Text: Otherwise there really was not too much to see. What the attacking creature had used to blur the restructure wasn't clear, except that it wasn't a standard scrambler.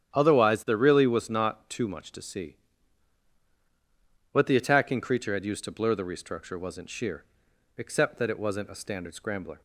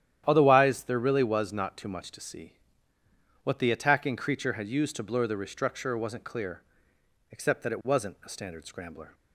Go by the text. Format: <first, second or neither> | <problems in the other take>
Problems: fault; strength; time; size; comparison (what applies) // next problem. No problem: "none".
second | starts louder than the rest; strong; until 1.1 s; 10 dB; strong in the second // says "sheer" for "clear"; at 6.8 s